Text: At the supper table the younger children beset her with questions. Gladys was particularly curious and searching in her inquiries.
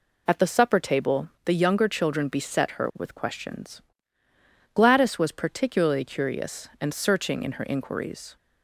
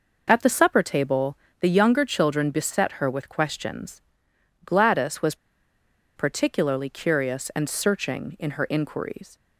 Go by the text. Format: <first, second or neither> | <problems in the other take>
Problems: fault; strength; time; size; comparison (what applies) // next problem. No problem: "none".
first | pauses between "table" and "the"; slight; at 1.3 s; 0.22 s long; slight in the first // pauses between "was" and "particularly"; noticeable; at 5.3 s; 0.81 s long